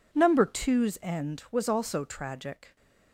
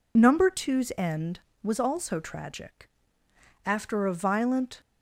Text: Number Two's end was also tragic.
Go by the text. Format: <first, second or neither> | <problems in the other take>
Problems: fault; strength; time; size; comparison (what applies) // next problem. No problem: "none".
first | goes on to say "After a violent"; noticeable; from 3.6 s on; 1.1 s long